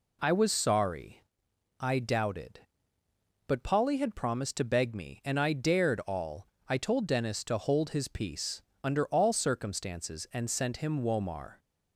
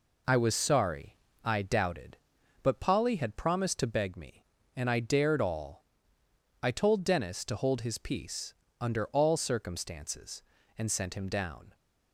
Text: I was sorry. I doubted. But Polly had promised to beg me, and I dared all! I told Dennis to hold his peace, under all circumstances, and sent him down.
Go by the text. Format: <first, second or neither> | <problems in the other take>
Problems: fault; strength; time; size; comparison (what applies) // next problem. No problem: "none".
second | says "womar" for "down"; at 11.0 s